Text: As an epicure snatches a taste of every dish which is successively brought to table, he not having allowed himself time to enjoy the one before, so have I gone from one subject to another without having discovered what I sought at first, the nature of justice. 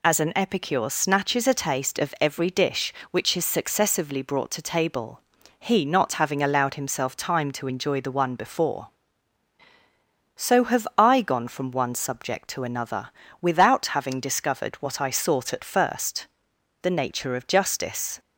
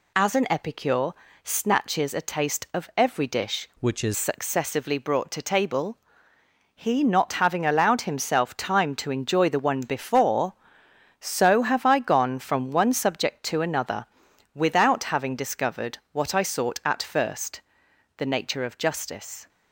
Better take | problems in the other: first | pauses between "epicure" and "snatches"; slight; at 1.1 s; 0.32 s long // changes voice from "which" to "is"; from 3.7 to 4.1 s; 0.4 s long // pauses between "another" and "without"; noticeable; at 14.0 s; 0.48 s long; slight in the first

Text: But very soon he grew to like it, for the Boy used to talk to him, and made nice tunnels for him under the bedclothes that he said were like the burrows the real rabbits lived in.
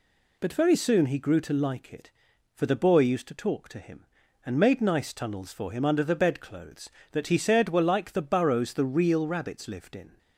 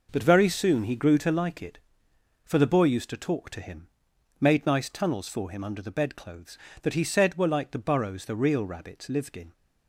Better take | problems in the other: first | skips "and"; at 4.1 s

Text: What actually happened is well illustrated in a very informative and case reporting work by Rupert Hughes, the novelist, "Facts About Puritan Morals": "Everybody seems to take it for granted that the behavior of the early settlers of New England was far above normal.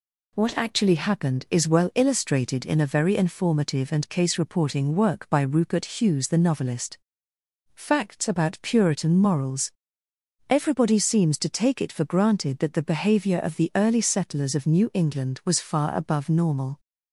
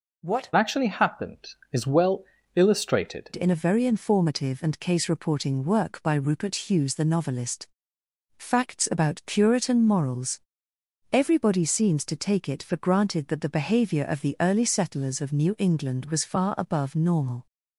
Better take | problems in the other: first | changes voice from "actually" to "illustrated"; from 0.5 to 3.3 s; 2.8 s long // pauses between "well" and "illustrated"; slight; at 2.2 s; 0.32 s long

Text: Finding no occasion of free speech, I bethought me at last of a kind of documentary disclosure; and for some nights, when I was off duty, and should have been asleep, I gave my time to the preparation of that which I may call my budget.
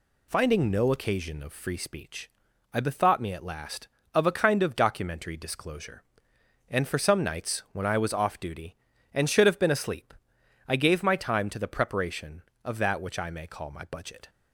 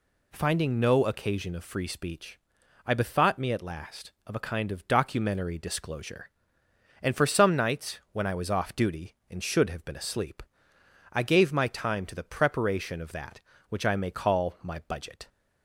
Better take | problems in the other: neither | none

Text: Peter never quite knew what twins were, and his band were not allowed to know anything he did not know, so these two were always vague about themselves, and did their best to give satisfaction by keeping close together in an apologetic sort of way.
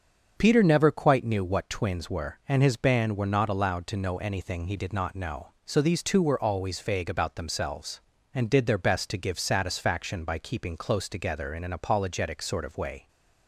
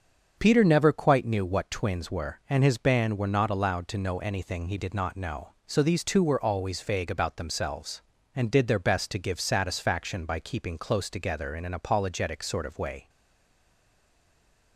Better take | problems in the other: first | starts louder than the rest; until 1.3 s; 6.5 dB; also in the first // stays silent after the last word; noticeable; from 13.0 s on; 1.7 s long

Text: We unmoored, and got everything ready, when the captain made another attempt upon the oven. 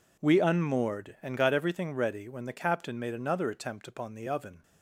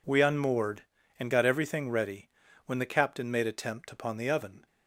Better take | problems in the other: first | skips "another"; at 3.4 s

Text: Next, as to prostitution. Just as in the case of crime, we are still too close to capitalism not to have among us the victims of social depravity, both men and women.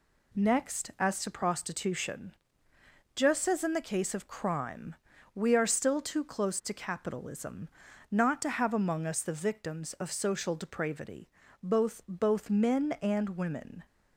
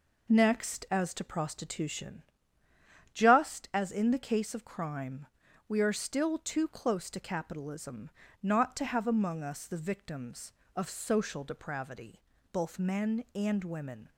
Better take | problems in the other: second | pauses between "capitalism" and "not"; at 7.6 s; 0.42 s long; slight in the second // says "both" twice; at 12.0 s

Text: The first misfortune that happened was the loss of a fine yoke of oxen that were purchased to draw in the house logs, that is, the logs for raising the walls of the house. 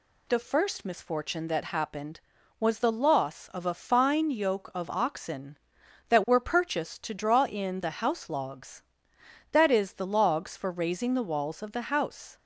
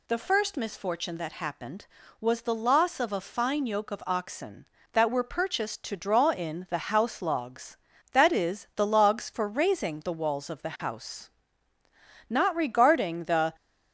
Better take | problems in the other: first | goes on to say "Not regarding the"; noticeable; from 12.2 s on; 1.2 s long

